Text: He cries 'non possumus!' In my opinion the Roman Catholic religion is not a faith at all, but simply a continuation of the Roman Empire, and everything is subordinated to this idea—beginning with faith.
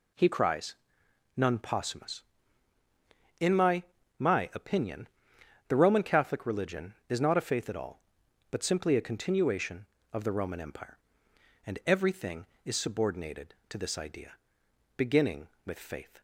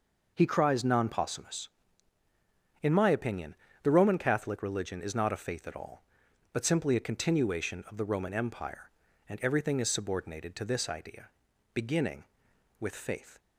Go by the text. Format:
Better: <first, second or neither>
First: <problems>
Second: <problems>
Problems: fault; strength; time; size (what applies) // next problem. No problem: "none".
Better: second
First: pauses between "cries" and "non"; noticeable; at 0.7 s; 0.62 s long // says "my" twice; at 4.1 s // pauses between "opinion" and "the"; noticeable; at 5.0 s; 0.60 s long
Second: pauses between "opinion" and "the"; slight; at 3.5 s; 0.28 s long